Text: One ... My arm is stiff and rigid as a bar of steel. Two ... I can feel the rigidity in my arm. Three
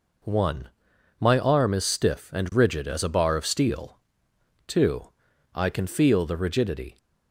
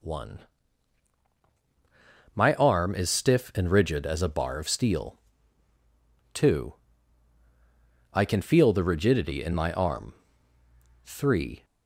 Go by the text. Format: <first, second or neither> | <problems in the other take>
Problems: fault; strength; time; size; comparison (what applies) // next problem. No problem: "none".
second | stops before "in my arm Three"; at 6.9 s